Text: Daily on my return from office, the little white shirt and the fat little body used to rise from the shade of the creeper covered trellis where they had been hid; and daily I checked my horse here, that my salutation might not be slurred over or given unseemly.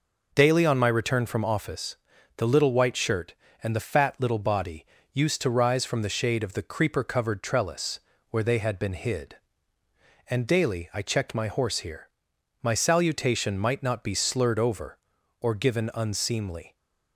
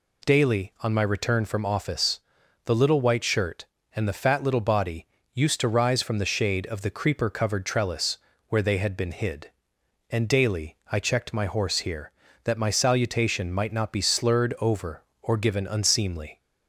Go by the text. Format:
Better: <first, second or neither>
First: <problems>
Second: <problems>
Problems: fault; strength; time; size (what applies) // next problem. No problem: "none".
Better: second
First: pauses between "body" and "used"; slight; at 4.8 s; 0.26 s long // pauses between "trellis" and "where"; slight; at 7.9 s; 0.30 s long // skips "that"; at 12.3 s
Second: pauses between "body" and "used"; slight; at 5.0 s; 0.28 s long // pauses between "trellis" and "where"; slight; at 8.1 s; 0.28 s long